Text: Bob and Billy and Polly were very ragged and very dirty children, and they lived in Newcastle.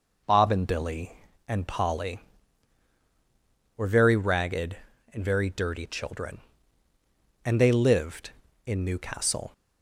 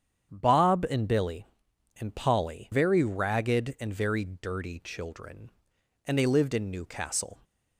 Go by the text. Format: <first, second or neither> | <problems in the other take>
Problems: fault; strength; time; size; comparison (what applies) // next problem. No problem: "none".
first | starts louder than the rest; strong; until 1.3 s; 8.5 dB // skips "were"; at 2.7 s